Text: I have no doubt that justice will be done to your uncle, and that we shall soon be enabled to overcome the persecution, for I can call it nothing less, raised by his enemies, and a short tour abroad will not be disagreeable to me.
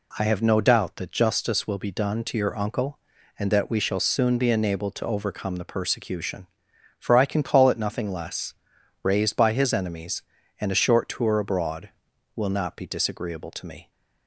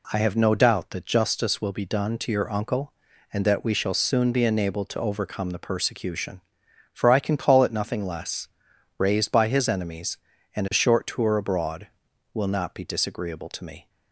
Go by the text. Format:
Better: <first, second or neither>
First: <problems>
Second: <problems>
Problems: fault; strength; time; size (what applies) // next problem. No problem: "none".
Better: neither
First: none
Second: none